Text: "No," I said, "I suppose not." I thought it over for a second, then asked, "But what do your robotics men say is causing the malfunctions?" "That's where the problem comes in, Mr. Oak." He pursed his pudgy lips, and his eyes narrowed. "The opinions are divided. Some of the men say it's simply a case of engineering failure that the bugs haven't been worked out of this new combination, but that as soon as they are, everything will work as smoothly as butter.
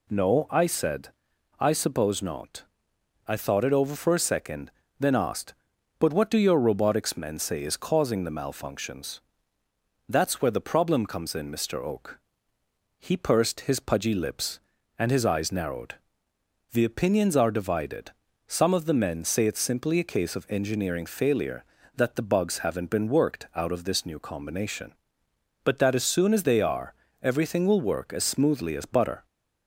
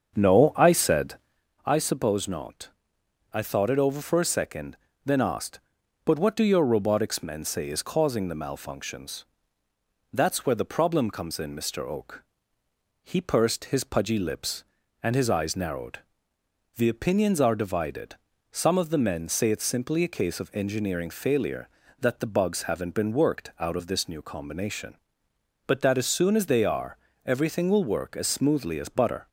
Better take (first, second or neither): first